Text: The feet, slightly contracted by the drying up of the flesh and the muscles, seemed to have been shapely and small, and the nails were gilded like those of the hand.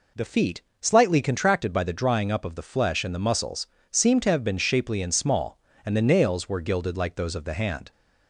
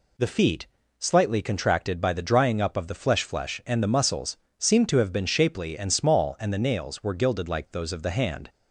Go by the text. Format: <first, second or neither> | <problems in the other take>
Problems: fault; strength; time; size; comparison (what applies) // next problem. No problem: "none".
first | says "flesh" twice; at 3.2 s